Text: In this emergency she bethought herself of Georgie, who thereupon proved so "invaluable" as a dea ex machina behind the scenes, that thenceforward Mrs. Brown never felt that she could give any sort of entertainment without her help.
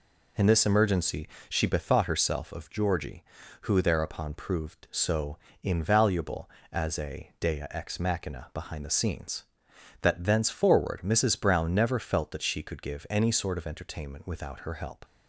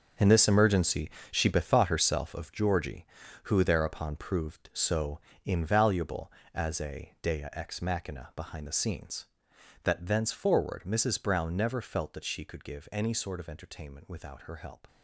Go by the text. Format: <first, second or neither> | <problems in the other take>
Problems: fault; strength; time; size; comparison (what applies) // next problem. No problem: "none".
first | gets quieter; strong; throughout; 12 dB // pauses between "emergency" and "she"; slight; at 1.1 s; 0.20 s long; slight in the first // pauses between "so" and "invaluable"; slight; at 5.1 s; 0.26 s long; slight in the first